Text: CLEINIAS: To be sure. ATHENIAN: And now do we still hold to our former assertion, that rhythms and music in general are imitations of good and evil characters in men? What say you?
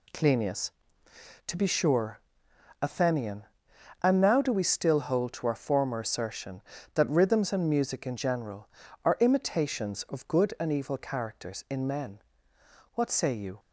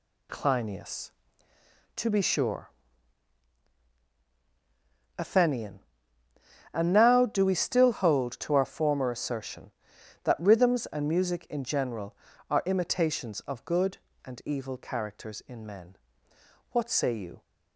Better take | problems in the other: neither | none

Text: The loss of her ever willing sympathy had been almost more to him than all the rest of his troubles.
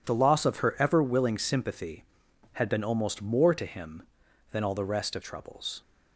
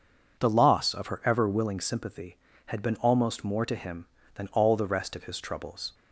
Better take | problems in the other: second | skips "his"; at 5.2 s

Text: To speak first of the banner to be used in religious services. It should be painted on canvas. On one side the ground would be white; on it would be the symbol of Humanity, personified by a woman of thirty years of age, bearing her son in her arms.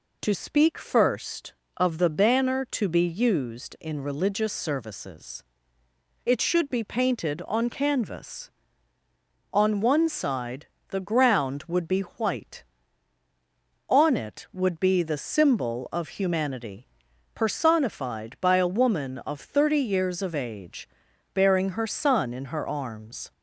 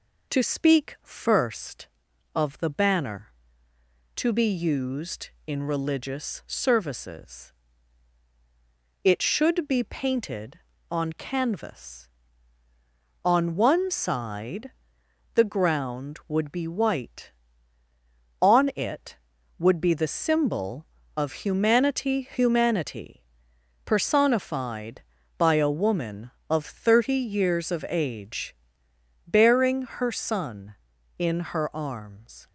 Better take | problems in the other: first | pauses between "side" and "the"; noticeable; at 14.7 s; 0.64 s long; slight in the first // says "Humanity" twice; at 22.3 s

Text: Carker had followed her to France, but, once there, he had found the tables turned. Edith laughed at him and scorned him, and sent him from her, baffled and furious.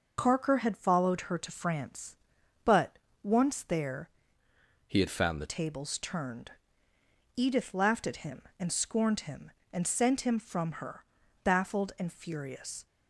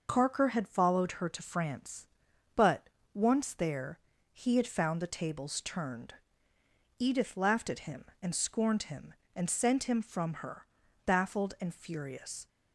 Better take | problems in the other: second | changes voice from "he" to "the"; from 4.8 to 5.4 s; 0.6 s long

